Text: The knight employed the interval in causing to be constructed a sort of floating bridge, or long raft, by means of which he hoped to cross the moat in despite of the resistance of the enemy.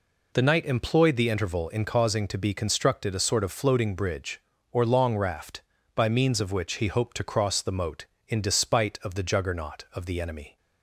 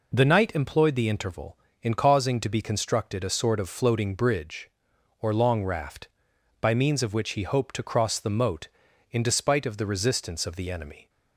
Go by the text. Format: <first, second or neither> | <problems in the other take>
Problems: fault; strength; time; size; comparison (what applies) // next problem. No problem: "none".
second | says "juggernaut" for "resistance"; at 9.2 s